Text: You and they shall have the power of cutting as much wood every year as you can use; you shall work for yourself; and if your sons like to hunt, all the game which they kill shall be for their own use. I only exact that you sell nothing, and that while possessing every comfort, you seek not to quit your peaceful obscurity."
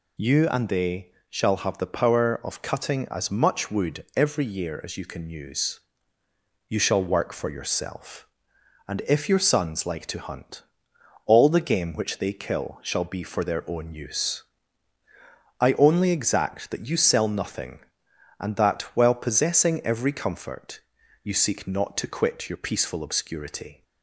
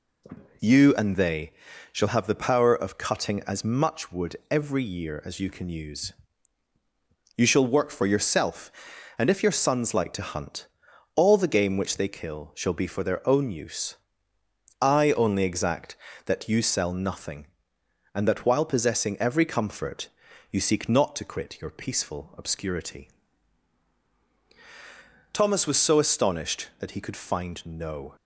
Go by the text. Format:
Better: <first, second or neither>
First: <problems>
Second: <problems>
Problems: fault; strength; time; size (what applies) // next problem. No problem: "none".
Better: first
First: pauses between "they" and "shall"; slight; at 1.1 s; 0.18 s long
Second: pauses between "they" and "shall"; at 1.5 s; 0.38 s long // goes on to say "Thomas was so astonished that he could find no"; strong; from 25.3 s on; 2.8 s long